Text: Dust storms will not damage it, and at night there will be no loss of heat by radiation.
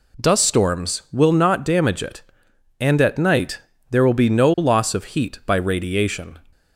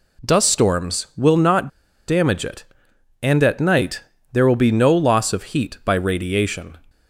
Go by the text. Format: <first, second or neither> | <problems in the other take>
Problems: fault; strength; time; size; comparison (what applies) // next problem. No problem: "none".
first | pauses between "not" and "damage"; at 1.6 s; 0.37 s long // pauses between "night" and "there"; slight; at 4.0 s; 0.30 s long; slight in the first